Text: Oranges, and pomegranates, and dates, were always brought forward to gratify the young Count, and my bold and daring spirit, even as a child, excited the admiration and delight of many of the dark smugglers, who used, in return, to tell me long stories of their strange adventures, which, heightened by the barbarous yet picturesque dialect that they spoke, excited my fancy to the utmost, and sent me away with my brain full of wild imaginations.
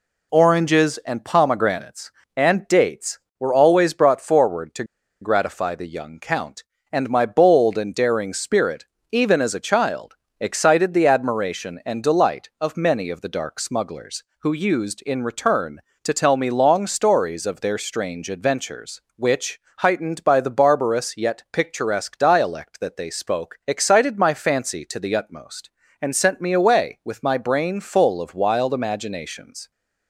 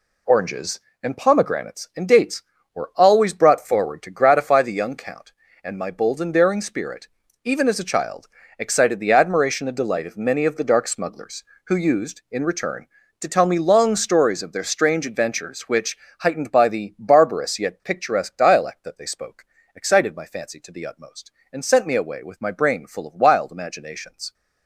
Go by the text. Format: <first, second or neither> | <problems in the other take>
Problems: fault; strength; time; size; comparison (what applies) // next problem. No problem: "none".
second | pauses between "to" and "gratify"; at 4.8 s; 0.37 s long